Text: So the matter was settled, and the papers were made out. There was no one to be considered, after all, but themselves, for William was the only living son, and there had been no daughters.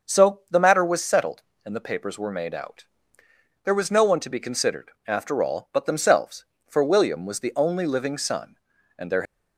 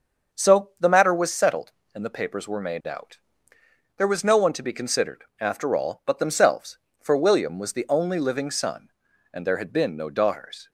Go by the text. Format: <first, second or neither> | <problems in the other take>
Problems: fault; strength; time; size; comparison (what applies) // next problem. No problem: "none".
second | starts louder than the rest; until 1.1 s; 6.5 dB; also in the second // stops before "had been no daughters"; at 9.2 s